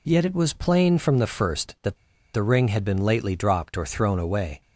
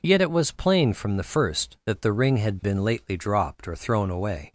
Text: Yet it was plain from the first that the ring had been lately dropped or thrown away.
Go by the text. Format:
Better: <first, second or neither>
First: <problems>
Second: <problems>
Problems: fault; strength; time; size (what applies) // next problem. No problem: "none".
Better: second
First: pauses between "that" and "the"; at 1.9 s; 0.37 s long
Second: none